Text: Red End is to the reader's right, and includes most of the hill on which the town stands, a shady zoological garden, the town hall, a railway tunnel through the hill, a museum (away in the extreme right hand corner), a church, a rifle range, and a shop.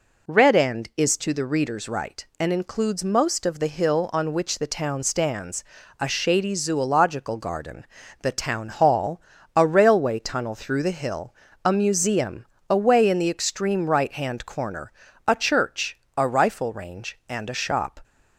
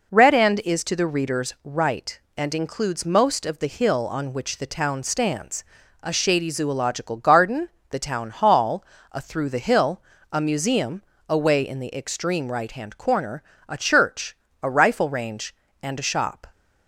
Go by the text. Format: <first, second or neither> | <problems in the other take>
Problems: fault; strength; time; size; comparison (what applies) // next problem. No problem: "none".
first | skips "railway tunnel"; at 9.2 s